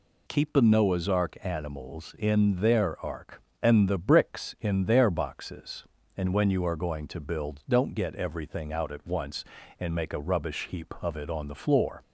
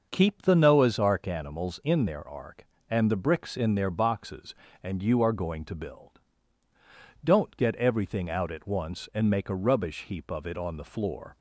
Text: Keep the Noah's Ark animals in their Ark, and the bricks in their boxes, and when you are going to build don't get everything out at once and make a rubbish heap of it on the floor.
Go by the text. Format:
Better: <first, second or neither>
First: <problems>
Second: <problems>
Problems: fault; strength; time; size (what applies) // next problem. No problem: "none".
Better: first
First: none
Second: starts louder than the rest; noticeable; until 1.1 s; 6 dB // skips "when"; at 5.0 s // pauses between "build" and "don't"; at 6.1 s; 1.1 s long